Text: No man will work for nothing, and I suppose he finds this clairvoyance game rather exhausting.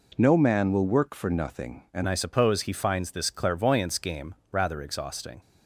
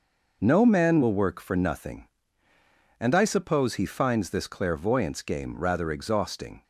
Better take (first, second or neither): second